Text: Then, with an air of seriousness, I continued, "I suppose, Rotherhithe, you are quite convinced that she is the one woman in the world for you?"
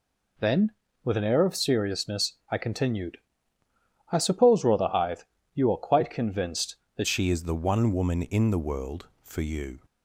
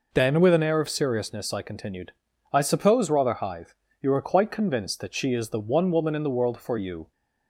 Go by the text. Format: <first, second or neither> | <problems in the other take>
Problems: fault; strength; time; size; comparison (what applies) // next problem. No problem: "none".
second | changes voice at "she"; from 7.0 s on; 2.8 s long